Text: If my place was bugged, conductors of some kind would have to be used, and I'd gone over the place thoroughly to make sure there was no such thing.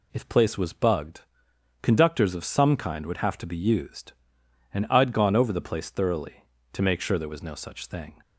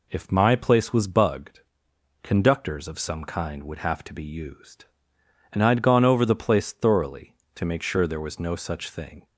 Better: second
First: skips "my"; at 0.2 s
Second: none

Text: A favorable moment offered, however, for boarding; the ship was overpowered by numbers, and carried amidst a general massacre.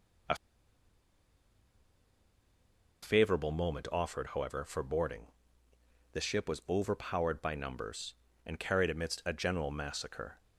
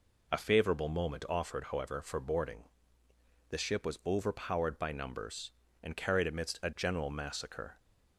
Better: second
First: pauses between "A" and "favorable"; strong; at 0.3 s; 2.6 s long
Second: none

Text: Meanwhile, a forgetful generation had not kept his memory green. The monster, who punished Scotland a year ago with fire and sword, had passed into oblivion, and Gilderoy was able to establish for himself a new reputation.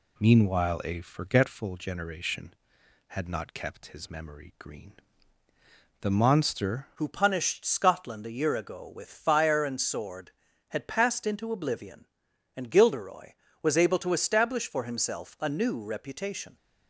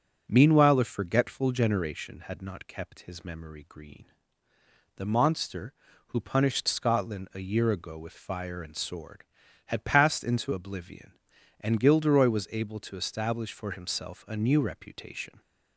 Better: second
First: changes voice at "who"; from 6.9 s on; 9.6 s long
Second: none

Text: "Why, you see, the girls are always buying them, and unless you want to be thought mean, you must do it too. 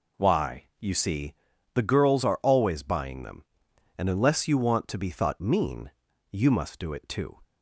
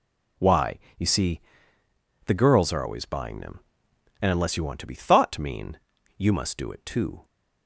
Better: neither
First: none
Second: none

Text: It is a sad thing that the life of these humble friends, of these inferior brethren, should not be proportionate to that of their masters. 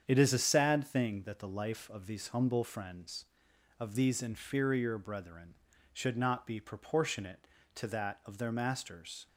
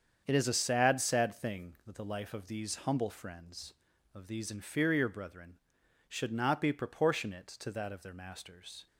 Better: first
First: starts louder than the rest; strong; until 1.0 s; 8 dB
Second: starts louder than the rest; strong; until 1.2 s; 7.5 dB // says "sad" twice; at 1.0 s

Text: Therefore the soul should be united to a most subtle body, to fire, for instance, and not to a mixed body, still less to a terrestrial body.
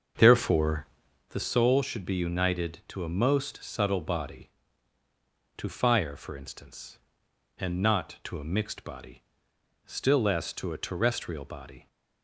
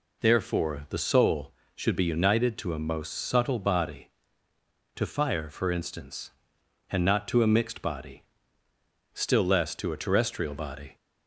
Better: second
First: starts louder than the rest; until 1.4 s; 6.5 dB // pauses between "Therefore" and "the"; at 0.8 s; 0.44 s long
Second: none

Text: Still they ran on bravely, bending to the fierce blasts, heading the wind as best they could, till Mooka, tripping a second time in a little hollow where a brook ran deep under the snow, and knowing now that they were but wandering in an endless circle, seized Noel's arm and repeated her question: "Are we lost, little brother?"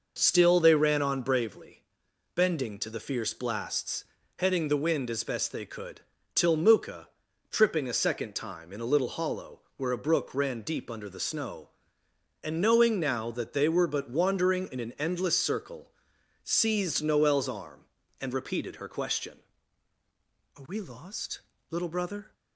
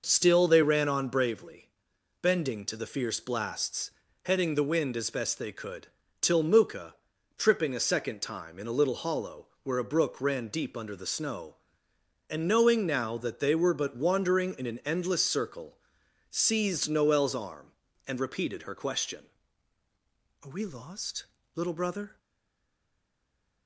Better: first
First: pauses between "hollow" and "where"; slight; at 9.6 s; 0.16 s long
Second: pauses between "hollow" and "where"; slight; at 9.4 s; 0.16 s long // stays silent after the last word; noticeable; from 22.1 s on; 1.5 s long

